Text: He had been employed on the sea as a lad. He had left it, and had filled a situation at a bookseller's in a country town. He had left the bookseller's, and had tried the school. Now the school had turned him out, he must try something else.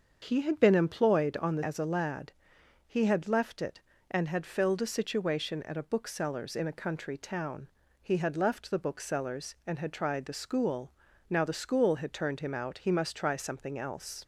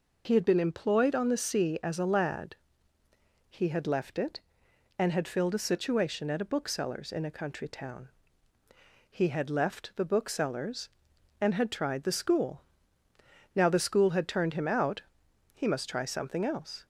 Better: second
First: starts louder than the rest; until 1.2 s; 6.5 dB // skips "sea"; at 1.6 s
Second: none

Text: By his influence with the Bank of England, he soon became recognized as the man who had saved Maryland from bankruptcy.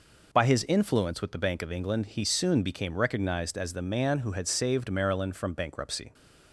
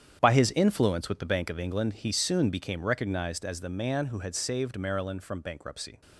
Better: first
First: none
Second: gets quieter; strong; throughout; 12.5 dB

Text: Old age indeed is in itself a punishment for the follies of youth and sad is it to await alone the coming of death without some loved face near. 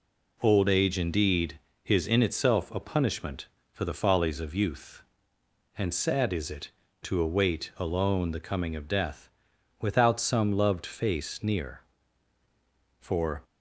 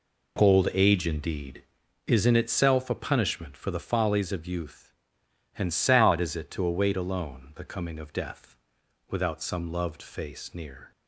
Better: second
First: pauses between "death" and "without"; noticeable; at 9.2 s; 0.52 s long // goes on to say "For"; slight; from 13.0 s on; 0.42 s long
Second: pauses between "death" and "without"; noticeable; at 8.5 s; 0.54 s long

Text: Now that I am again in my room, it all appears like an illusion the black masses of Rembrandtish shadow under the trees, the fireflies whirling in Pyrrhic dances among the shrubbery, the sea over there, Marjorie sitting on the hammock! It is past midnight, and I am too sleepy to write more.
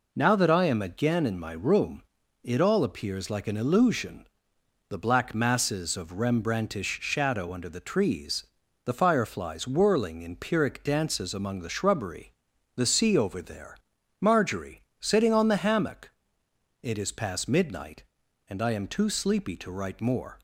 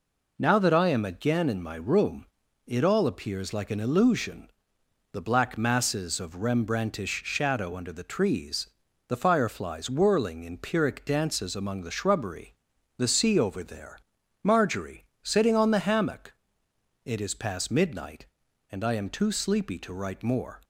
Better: neither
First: pauses between "illusion" and "the"; noticeable; at 4.2 s; 0.62 s long // pauses between "Marjorie" and "sitting"; slight; at 14.8 s; 0.18 s long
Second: pauses between "illusion" and "the"; noticeable; at 4.4 s; 0.62 s long // pauses between "Marjorie" and "sitting"; slight; at 15.0 s; 0.18 s long

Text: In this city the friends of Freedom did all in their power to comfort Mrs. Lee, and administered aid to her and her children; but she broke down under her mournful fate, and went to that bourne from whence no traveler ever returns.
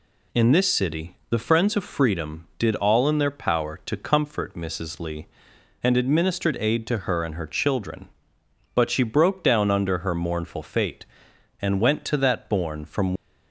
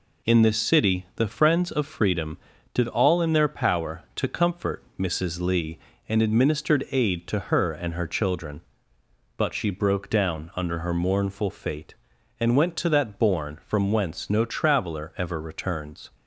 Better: second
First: stops before "whence no traveler ever returns"; at 13.1 s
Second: none

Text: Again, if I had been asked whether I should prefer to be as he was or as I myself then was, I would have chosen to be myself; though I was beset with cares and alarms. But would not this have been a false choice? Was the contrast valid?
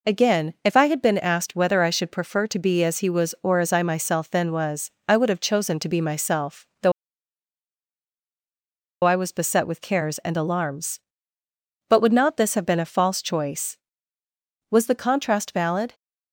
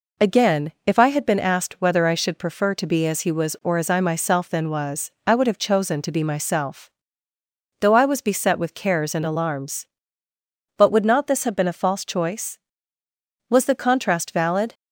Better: second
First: pauses between "though" and "I"; strong; at 6.9 s; 2.1 s long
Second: none

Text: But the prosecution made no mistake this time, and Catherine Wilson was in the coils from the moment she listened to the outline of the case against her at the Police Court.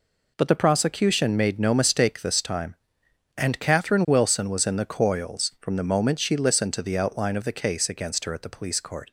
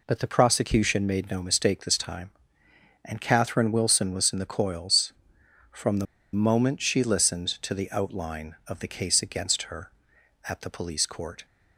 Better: first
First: none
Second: pauses between "the" and "moment"; slight; at 6.0 s; 0.27 s long

